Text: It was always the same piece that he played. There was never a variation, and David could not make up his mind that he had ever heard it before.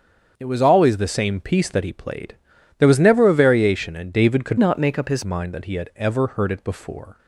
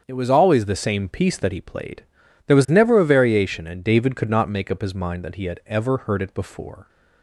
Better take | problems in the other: second | starts louder than the rest; until 1.3 s; 7 dB; strong in the second // changes voice from "not" to "his"; from 4.5 to 5.2 s; 0.7 s long

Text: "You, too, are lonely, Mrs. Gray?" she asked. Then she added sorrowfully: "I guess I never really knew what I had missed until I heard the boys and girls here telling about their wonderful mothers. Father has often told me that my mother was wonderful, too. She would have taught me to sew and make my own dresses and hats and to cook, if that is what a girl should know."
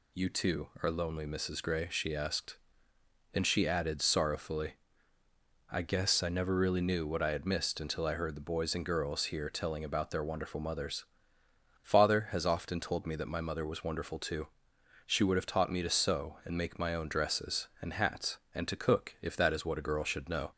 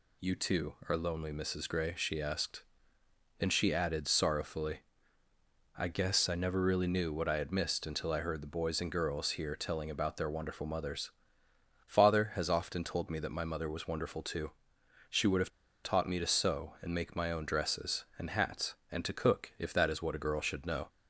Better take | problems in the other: first | pauses between "have" and "taught"; slight; at 15.5 s; 0.33 s long

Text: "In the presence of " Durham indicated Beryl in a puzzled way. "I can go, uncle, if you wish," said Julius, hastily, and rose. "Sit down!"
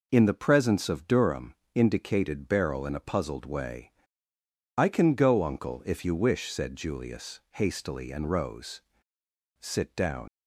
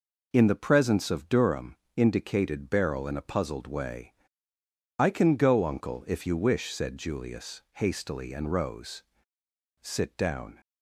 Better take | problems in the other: second | pauses between "Durham" and "indicated"; slight; at 1.5 s; 0.18 s long; slight in the second // leaves "down" unfinished; at 10.2 s; 105 ms

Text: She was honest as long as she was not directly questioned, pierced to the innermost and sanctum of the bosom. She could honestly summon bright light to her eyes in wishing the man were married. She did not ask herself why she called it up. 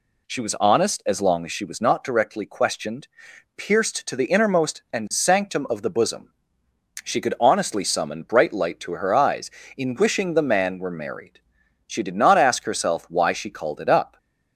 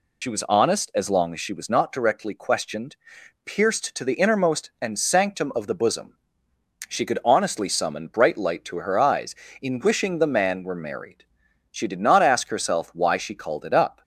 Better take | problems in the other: first | loses the start of "She"; at 0.2 s; 70 ms

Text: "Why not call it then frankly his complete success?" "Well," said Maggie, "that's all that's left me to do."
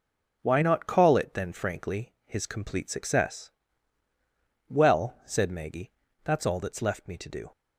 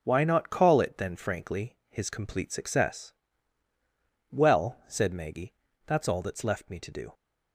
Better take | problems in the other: neither | none

